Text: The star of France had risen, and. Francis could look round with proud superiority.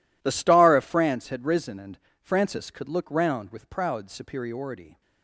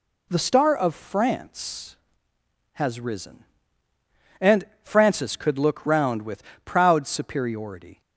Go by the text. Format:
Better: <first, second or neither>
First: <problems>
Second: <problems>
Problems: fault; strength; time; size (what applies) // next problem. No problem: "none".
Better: first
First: none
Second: says "has" for "had"; at 2.7 s // pauses between "with" and "proud"; slight; at 6.4 s; 0.22 s long